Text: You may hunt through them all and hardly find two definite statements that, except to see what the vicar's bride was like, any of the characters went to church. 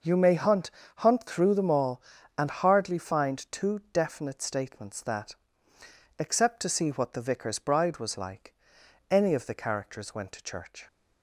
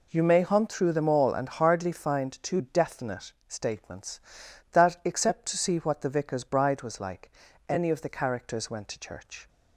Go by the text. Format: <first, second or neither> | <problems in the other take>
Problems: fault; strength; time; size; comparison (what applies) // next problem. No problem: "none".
second | says "hunt" twice; at 0.9 s